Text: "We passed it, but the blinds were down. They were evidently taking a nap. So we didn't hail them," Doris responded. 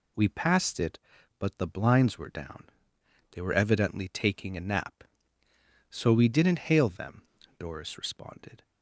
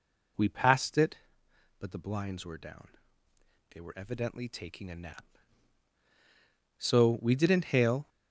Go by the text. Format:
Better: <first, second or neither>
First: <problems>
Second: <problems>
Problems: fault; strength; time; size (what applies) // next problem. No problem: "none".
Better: first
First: none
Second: stops before "them Doris responded"; at 8.0 s